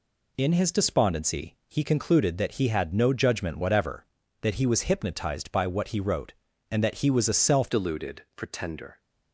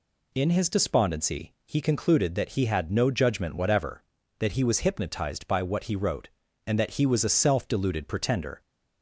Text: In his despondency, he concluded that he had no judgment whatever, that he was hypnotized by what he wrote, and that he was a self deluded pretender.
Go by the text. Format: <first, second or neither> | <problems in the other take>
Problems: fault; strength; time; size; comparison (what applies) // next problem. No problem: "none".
second | changes voice at "deluded"; from 7.7 s on; 1.2 s long